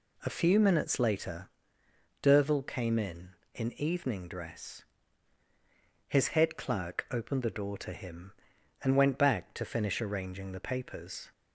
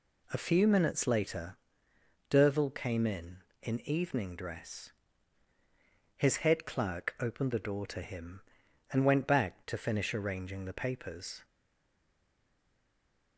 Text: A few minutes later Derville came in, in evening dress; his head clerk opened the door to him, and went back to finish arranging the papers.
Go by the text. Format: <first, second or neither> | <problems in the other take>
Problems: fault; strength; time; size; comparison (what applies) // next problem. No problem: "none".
first | pauses between "later" and "Derville"; noticeable; at 1.5 s; 0.72 s long; noticeable in the first // stays silent after the last word; noticeable; from 11.4 s on; 1.9 s long